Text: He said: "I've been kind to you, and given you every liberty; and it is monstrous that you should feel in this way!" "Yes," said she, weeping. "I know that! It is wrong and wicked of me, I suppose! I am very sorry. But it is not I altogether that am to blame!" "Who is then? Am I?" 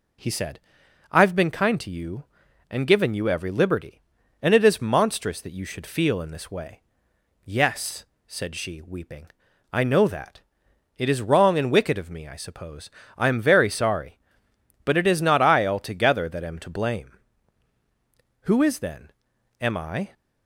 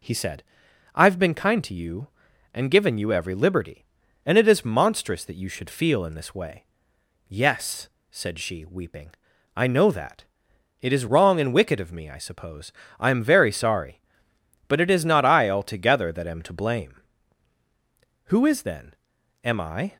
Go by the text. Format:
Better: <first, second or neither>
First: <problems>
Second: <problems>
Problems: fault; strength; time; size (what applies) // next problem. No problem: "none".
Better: neither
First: none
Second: none